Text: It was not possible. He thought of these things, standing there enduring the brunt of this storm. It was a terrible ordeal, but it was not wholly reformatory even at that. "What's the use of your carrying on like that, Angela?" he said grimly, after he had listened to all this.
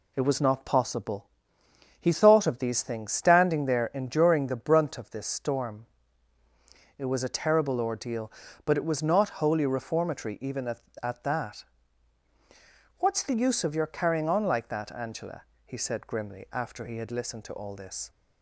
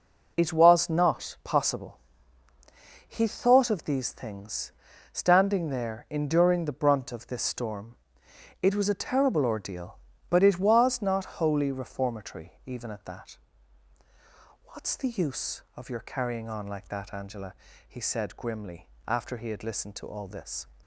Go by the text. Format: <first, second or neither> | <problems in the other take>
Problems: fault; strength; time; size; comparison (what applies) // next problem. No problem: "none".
second | says "at" twice; at 11.0 s